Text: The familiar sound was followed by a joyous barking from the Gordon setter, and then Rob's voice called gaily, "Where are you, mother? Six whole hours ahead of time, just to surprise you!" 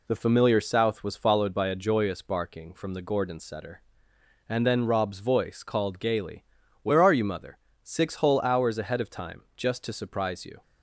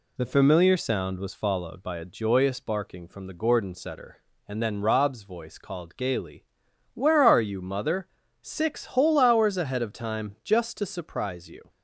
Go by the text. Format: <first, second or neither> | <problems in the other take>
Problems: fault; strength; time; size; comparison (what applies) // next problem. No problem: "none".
second | says "south" for "sound"; at 0.5 s